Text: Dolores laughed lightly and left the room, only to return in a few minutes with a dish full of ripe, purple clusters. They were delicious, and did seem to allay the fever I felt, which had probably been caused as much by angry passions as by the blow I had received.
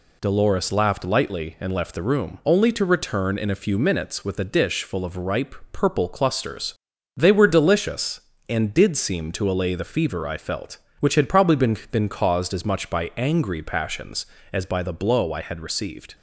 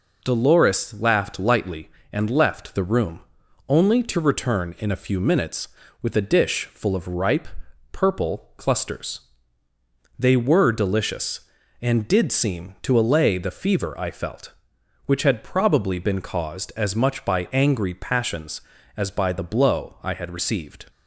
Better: second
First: says "been" twice; at 11.9 s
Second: none

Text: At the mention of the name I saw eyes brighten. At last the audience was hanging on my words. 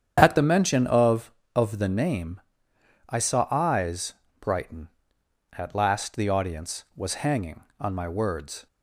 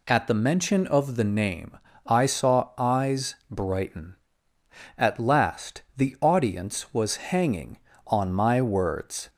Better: second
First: starts louder than the rest; strong; until 1.2 s; 8.5 dB // says "of" twice; at 1.5 s // pauses between "name" and "I"; noticeable; at 2.4 s; 0.68 s long // pauses between "eyes" and "brighten"; slight; at 4.1 s; 0.26 s long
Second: pauses between "name" and "I"; slight; at 1.7 s; 0.28 s long

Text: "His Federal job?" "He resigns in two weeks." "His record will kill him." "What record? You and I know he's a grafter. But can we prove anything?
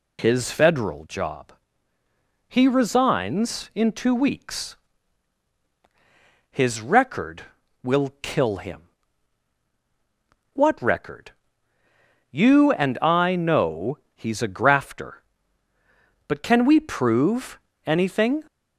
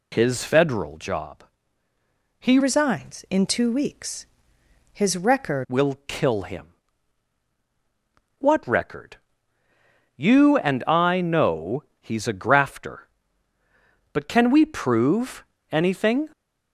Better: first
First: pauses between "know" and "he's"; slight; at 13.9 s; 0.16 s long // pauses between "prove" and "anything"; slight; at 17.5 s; 0.26 s long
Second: changes voice from "resigns" to "record"; from 2.6 to 5.6 s; 3.0 s long // pauses between "know" and "he's"; slight; at 11.8 s; 0.16 s long // pauses between "prove" and "anything"; slight; at 15.4 s; 0.26 s long

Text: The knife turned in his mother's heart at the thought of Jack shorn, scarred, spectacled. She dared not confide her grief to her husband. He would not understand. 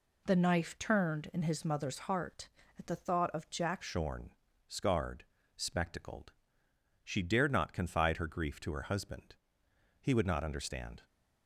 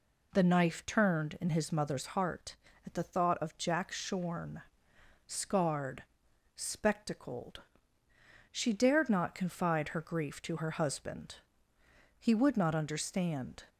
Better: second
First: changes voice at "shorn"; from 3.8 s on; 7.2 s long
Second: none

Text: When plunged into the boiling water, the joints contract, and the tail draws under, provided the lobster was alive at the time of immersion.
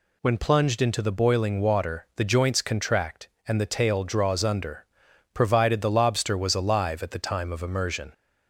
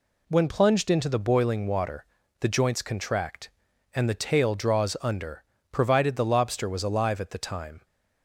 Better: first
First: none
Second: stops before "of immersion"; at 7.8 s

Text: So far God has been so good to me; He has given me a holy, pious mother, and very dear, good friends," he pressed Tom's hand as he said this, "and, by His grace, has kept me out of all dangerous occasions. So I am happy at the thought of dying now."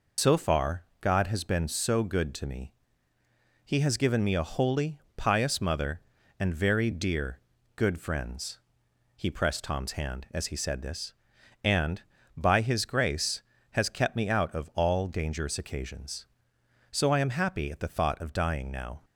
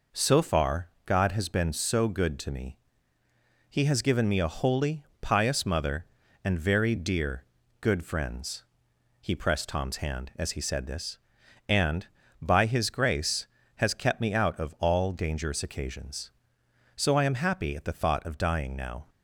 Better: second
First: loses the start of "So"; at 0.1 s; 105 ms // pauses between "far" and "God"; slight; at 0.8 s; 0.18 s long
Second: pauses between "far" and "God"; slight; at 0.8 s; 0.18 s long

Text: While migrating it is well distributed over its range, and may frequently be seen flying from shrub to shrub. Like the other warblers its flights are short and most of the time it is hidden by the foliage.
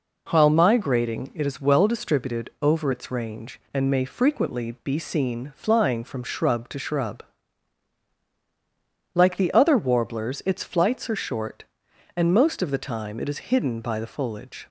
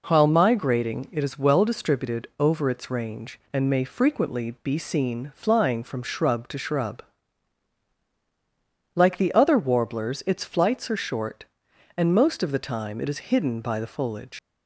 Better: first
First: none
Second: leaves "foliage" unfinished; at 14.3 s; 90 ms

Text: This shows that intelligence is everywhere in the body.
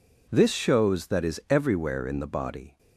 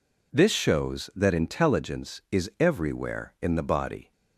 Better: second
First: skips "intelligence"; at 1.2 s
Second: none

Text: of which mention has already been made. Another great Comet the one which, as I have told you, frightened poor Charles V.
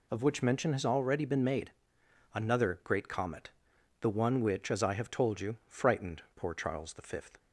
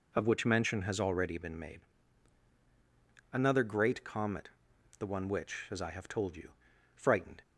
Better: first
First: pauses between "Comet" and "the"; noticeable; at 3.5 s; 0.50 s long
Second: pauses between "Comet" and "the"; noticeable; at 4.4 s; 0.50 s long // stops before "poor Charles V"; at 7.4 s

